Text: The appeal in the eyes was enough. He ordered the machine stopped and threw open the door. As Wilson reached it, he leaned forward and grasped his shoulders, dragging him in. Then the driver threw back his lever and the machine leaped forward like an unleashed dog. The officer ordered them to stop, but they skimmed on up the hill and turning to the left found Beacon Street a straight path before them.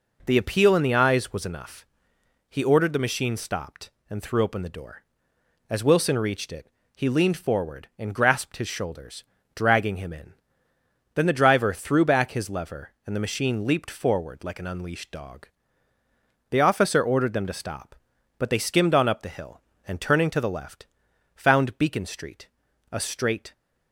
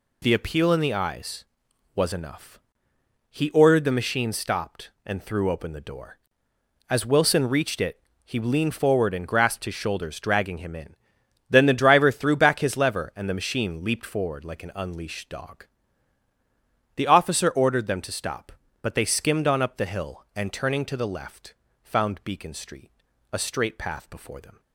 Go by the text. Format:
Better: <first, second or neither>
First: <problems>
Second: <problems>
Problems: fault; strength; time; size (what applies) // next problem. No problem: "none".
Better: second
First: pauses between "left" and "found"; noticeable; at 20.8 s; 0.48 s long // pauses between "Street" and "a"; at 22.4 s; 0.44 s long // stops before "path before them"; at 23.5 s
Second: pauses between "left" and "found"; slight; at 21.5 s; 0.28 s long // pauses between "Street" and "a"; at 22.9 s; 0.40 s long